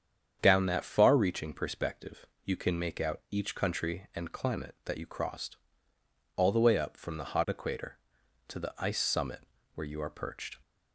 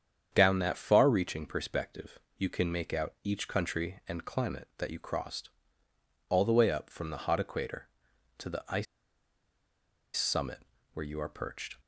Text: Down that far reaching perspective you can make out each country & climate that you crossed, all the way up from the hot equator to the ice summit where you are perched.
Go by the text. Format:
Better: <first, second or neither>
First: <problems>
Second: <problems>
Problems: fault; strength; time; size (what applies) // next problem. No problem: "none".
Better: first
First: starts louder than the rest; strong; until 1.4 s; 8 dB // pauses between "perspective" and "you"; slight; at 2.2 s; 0.20 s long // pauses between "summit" and "where"; slight; at 9.3 s; 0.36 s long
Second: starts louder than the rest; strong; until 1.3 s; 8 dB // pauses between "perspective" and "you"; slight; at 2.1 s; 0.20 s long // pauses between "ice" and "summit"; strong; at 8.8 s; 1.3 s long // pauses between "summit" and "where"; slight; at 10.5 s; 0.36 s long